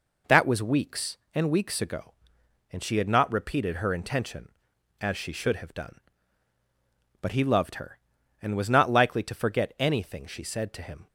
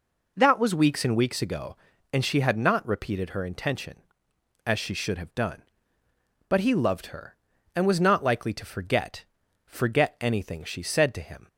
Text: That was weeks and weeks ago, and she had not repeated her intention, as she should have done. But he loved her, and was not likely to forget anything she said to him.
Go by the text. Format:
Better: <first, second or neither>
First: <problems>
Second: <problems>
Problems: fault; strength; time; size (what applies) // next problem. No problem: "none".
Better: first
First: none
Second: says "forget" twice; at 9.6 s